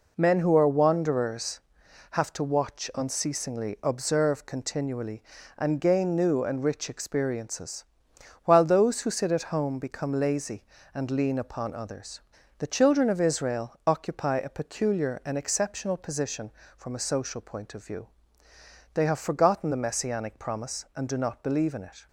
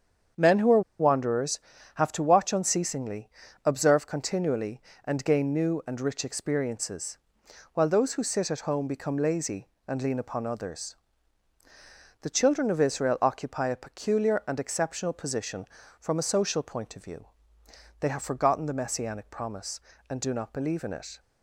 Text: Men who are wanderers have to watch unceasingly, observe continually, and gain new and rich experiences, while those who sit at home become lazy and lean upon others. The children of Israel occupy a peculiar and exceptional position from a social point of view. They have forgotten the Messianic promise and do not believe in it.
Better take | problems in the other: first | starts louder than the rest; strong; until 1.5 s; 7.5 dB // pauses between "are" and "wanderers"; slight; at 0.8 s; 0.18 s long

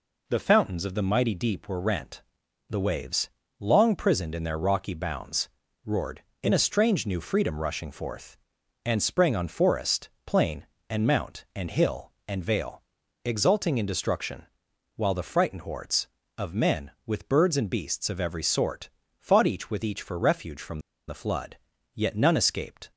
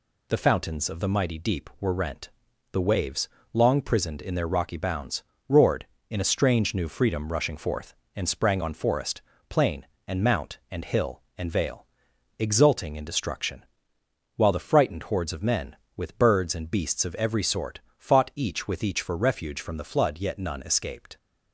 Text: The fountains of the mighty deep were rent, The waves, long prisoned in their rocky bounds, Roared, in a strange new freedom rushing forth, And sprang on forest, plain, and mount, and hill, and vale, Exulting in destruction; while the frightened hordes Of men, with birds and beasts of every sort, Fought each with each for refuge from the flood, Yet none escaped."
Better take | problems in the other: second | pauses between "from" and "the"; slight; at 20.7 s; 0.28 s long

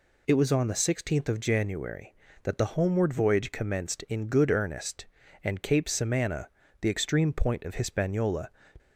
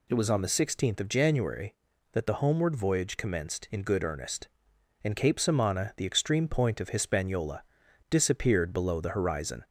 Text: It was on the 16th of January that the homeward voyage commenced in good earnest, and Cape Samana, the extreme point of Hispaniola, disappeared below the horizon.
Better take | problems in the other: second | stops before "disappeared below the horizon"; at 8.7 s

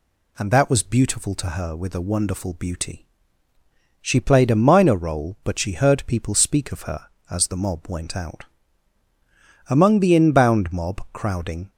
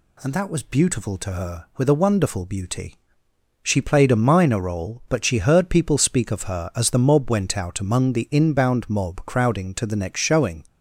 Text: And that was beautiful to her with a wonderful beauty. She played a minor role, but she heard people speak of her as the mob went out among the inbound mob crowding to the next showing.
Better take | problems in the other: second | pauses between "out" and "among"; at 8.4 s; 1.2 s long // stops before "to the next showing"; at 11.7 s

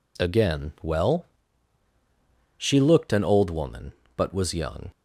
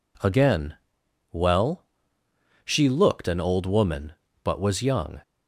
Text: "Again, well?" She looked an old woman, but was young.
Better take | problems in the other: neither | none

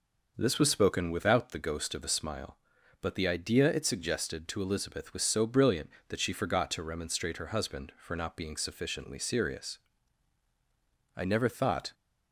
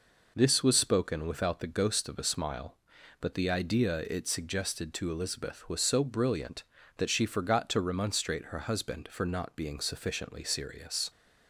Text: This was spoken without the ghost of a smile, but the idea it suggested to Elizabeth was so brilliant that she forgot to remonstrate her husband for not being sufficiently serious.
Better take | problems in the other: second | goes on to say "I never thought"; noticeable; from 11.1 s on; 0.78 s long

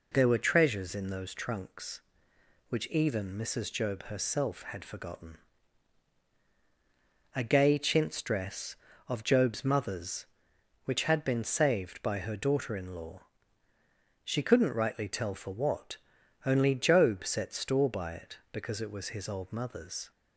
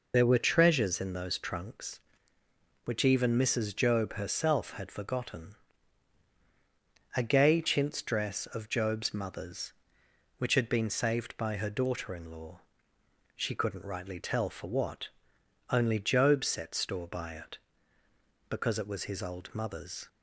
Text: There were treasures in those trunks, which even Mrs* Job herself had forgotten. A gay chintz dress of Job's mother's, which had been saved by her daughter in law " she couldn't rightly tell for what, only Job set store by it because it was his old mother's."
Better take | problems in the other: first | loses the start of "There"; at 0.1 s; 35 ms

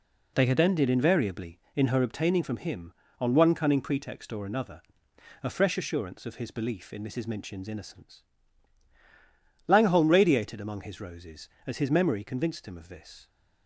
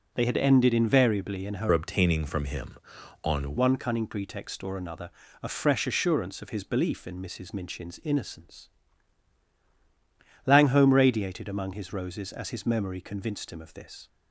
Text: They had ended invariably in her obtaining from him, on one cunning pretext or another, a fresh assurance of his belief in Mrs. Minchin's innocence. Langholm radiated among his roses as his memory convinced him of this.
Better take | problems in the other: first | changes voice from "obtaining" to "on"; from 1.7 to 3.5 s; 1.8 s long

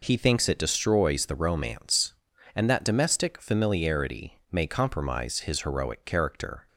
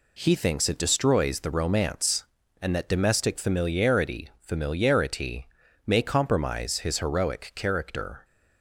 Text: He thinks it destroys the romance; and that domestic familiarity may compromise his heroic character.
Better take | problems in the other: first | says "familiarity" twice; at 4.4 s

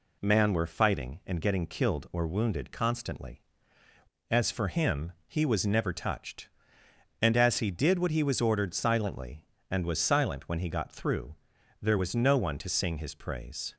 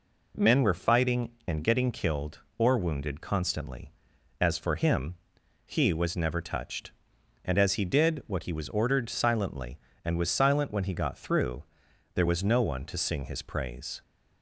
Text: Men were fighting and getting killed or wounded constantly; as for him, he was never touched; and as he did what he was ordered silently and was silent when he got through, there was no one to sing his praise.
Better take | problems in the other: second | says "Man" for "Men"; at 0.2 s

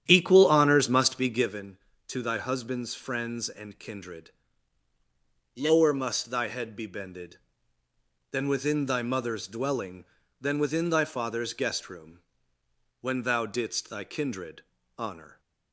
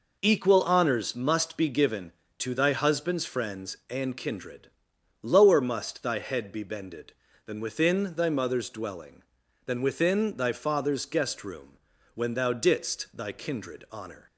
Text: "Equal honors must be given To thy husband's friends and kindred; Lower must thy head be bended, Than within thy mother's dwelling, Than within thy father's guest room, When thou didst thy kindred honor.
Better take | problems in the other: second | starts louder than the rest; strong; until 1.6 s; 10 dB // pauses between "kindred" and "honor"; slight; at 14.6 s; 0.34 s long

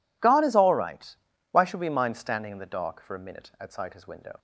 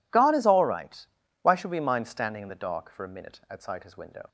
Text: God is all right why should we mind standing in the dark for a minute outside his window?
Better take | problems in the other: neither | pauses between "right" and "why"; slight; the same in both

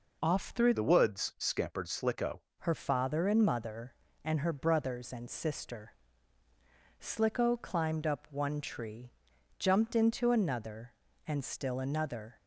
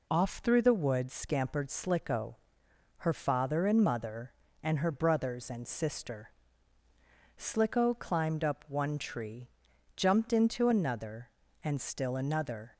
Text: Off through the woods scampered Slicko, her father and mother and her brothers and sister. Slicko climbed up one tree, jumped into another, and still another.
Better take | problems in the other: second | changes voice from "the" to "Slicko"; from 0.7 to 2.4 s; 1.7 s long

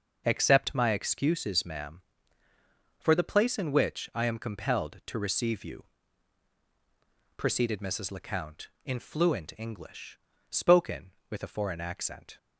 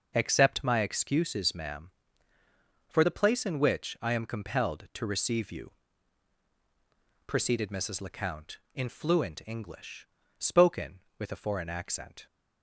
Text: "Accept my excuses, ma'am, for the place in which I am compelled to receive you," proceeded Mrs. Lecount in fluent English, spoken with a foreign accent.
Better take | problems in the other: neither | none

